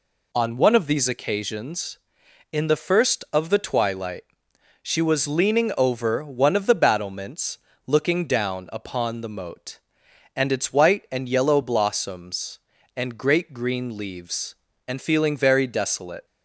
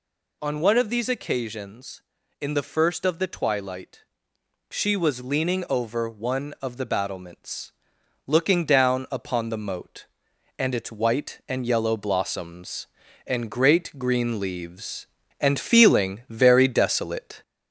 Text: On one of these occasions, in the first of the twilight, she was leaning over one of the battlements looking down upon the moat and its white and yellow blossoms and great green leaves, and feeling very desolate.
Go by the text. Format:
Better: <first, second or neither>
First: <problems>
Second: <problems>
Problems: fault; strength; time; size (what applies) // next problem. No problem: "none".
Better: first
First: pauses between "battlements" and "looking"; slight; at 7.5 s; 0.28 s long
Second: gets louder; slight; throughout; 3 dB // pauses between "battlements" and "looking"; noticeable; at 7.7 s; 0.54 s long